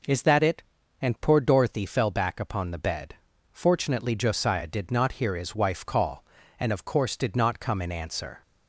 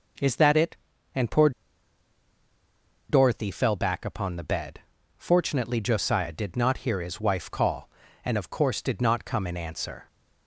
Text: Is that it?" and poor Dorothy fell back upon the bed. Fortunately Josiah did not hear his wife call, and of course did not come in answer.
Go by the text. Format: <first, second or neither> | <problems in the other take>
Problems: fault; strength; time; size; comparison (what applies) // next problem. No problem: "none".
first | pauses between "poor" and "Dorothy"; strong; at 1.5 s; 1.5 s long